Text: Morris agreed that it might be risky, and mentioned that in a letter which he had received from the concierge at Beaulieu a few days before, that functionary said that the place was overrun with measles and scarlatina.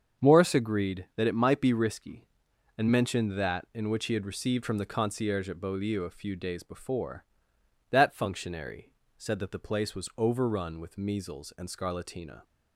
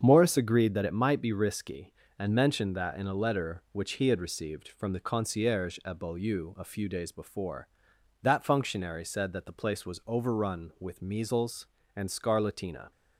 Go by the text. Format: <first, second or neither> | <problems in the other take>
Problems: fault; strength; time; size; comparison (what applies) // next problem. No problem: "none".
second | starts louder than the rest; until 1.2 s; 7 dB; strong in the second // skips "a letter"; at 3.9 s // pauses between "functionary" and "said"; slight; at 8.9 s; 0.26 s long